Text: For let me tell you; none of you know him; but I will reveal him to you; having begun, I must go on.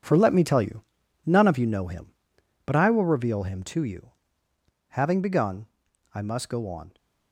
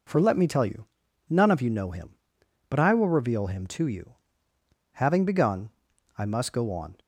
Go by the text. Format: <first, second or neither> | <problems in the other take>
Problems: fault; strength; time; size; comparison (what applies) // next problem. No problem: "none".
second | gets quieter; strong; throughout; 9.5 dB